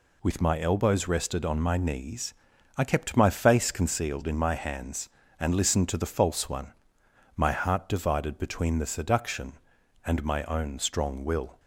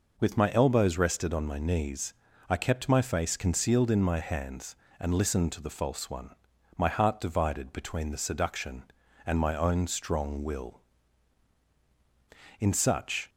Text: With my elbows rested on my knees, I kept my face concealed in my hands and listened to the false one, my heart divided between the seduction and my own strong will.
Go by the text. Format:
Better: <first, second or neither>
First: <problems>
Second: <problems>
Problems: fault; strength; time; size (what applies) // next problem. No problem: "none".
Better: first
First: none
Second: goes on to say "In such"; noticeable; from 12.5 s on; 0.70 s long